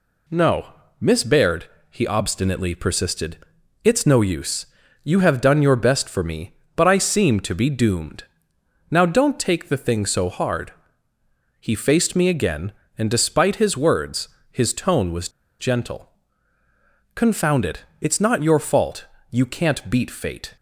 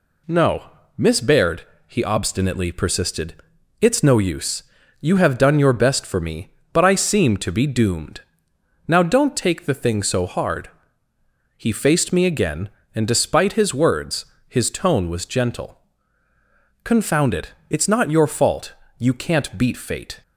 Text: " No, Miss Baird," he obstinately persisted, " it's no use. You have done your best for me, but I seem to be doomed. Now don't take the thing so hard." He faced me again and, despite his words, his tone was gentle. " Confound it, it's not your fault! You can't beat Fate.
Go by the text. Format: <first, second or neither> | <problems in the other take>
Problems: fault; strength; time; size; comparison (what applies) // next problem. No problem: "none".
second | pauses between "was" and "gentle"; slight; at 15.2 s; 0.29 s long